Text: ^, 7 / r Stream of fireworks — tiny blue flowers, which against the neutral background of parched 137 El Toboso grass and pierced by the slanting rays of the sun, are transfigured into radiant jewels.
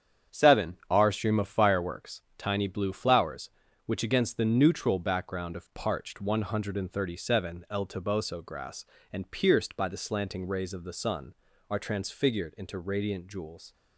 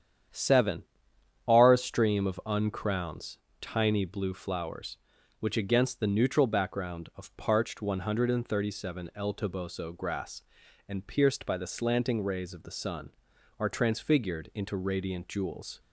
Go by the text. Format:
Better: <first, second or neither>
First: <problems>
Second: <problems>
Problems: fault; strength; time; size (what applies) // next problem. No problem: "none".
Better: first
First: starts louder than the rest; strong; until 1.4 s; 8.5 dB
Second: starts louder than the rest; strong; until 1.9 s; 9 dB // says "uncrowns" for "fireworks"; at 2.4 s